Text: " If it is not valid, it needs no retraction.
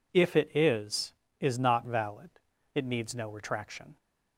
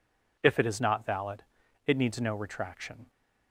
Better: second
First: says "is" twice; at 1.3 s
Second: none

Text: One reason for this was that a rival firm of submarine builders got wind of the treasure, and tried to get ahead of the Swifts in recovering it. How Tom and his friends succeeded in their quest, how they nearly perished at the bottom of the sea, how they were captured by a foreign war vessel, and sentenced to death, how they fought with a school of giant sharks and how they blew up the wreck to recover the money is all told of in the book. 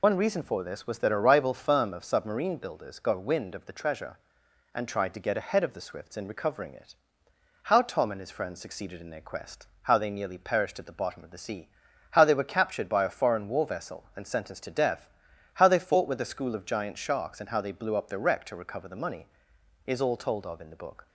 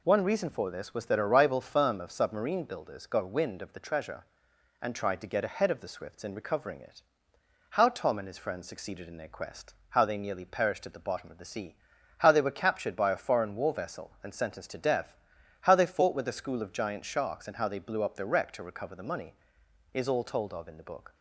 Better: second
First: loses the start of "One"; at 0.0 s; 65 ms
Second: none

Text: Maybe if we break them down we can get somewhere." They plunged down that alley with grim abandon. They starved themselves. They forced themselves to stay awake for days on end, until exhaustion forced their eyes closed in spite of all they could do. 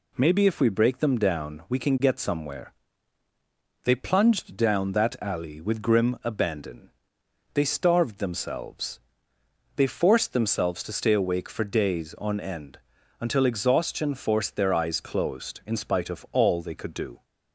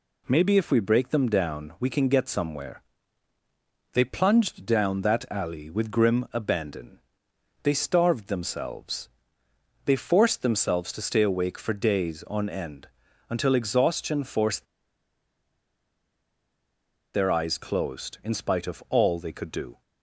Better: first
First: none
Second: pauses between "forced" and "their"; strong; at 14.6 s; 2.4 s long

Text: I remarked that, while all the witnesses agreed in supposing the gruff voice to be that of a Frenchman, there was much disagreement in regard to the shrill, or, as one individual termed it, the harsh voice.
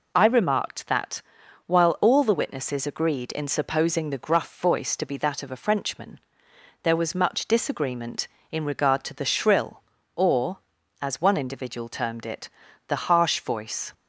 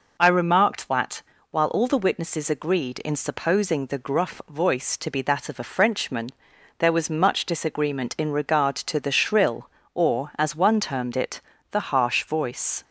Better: first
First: none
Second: skips "individual"; at 10.7 s

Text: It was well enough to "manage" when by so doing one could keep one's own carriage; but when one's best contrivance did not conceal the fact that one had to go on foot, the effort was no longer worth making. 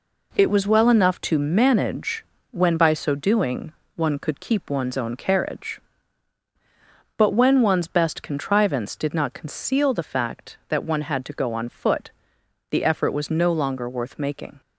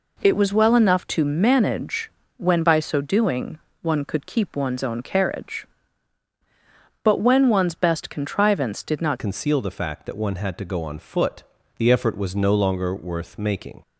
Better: first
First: pauses between "manage" and "when"; slight; at 2.2 s; 0.28 s long // pauses between "doing" and "one"; slight; at 3.7 s; 0.22 s long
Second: pauses between "manage" and "when"; slight; at 2.0 s; 0.28 s long // pauses between "doing" and "one"; slight; at 3.5 s; 0.22 s long // changes voice at "conceal"; from 9.1 s on; 4.7 s long

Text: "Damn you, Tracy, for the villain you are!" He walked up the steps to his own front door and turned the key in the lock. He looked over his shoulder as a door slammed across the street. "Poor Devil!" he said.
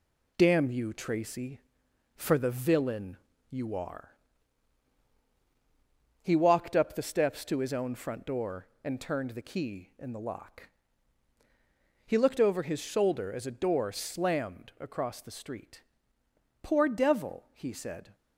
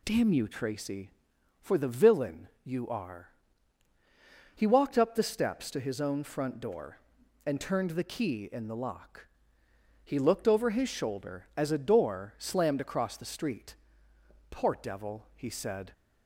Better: second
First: gets quieter; noticeable; throughout; 4.5 dB // pauses between "villain" and "you"; slight; at 3.1 s; 0.34 s long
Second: none

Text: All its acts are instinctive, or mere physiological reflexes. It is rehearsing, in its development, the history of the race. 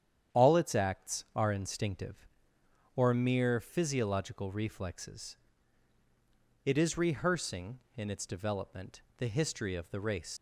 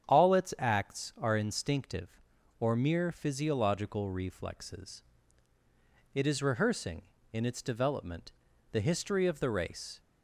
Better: second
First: starts louder than the rest; strong; until 1.4 s; 9 dB // leaves "race" unfinished; at 10.3 s; 95 ms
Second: starts louder than the rest; strong; until 1.1 s; 8.5 dB

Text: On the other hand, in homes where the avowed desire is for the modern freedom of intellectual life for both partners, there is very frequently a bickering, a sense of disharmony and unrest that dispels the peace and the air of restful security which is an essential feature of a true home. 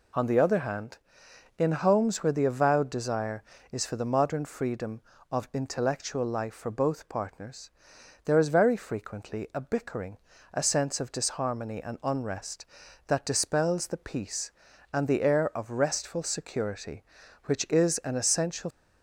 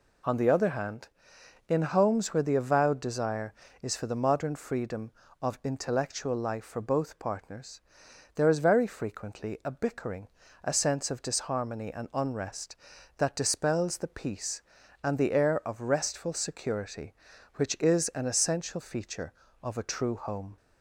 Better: second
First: stops before "feature of a true home"; at 18.6 s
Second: none

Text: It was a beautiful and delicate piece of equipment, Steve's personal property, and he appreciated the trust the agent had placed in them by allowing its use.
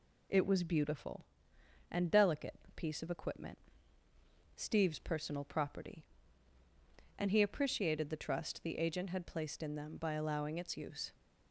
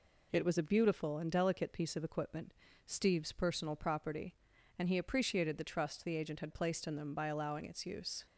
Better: second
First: skips "a"; at 0.6 s // pauses between "delicate" and "piece"; slight; at 2.5 s; 0.18 s long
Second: none

